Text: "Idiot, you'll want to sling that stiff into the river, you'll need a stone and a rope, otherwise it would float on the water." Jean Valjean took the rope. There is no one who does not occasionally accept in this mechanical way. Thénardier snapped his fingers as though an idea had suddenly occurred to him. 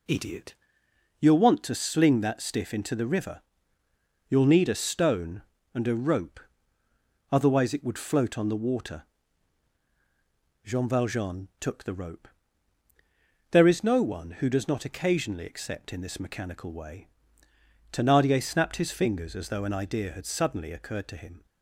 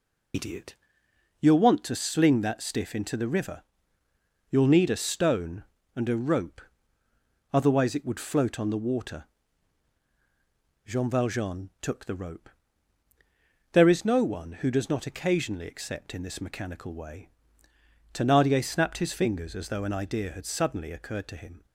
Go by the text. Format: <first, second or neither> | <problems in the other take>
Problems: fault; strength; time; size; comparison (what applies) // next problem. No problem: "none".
first | loses the start of "Idiot"; at 0.3 s; 60 ms